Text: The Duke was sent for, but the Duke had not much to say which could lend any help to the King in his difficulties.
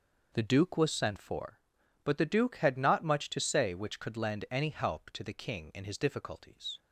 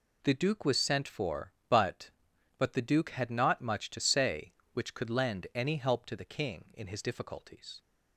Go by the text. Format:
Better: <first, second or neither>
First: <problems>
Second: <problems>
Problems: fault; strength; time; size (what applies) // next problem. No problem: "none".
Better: first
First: none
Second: says "but" twice; at 2.5 s